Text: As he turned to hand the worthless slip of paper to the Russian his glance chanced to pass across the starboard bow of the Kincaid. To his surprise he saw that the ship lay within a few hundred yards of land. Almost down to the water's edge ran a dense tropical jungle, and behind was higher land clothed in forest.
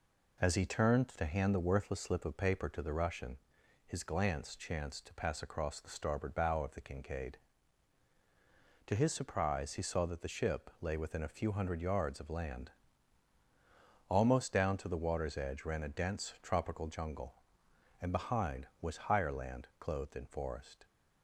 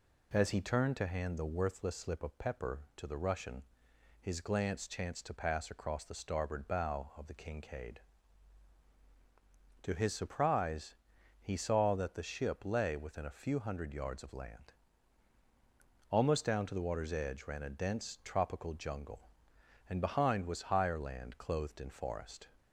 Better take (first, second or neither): first